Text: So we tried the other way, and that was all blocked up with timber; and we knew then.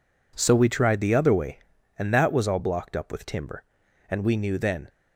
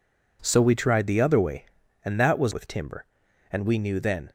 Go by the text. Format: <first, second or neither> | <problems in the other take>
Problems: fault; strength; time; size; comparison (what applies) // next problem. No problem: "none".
first | skips "all blocked up"; at 2.5 s